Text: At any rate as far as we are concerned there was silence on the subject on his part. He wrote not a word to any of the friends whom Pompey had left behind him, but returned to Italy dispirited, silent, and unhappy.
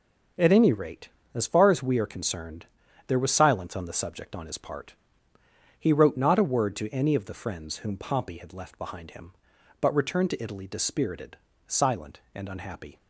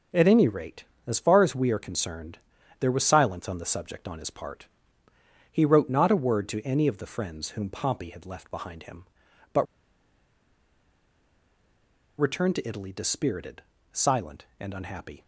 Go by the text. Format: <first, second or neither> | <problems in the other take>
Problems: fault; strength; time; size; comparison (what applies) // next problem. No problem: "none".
first | pauses between "concerned" and "there"; at 2.3 s; 0.42 s long; also in the first // pauses between "but" and "returned"; strong; at 9.6 s; 2.5 s long